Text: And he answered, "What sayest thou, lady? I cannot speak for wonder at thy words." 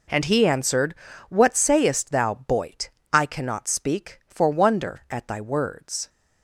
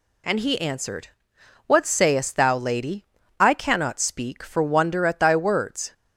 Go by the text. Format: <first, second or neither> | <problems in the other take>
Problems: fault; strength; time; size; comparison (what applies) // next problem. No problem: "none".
second | says "boyt" for "lady"; at 2.4 s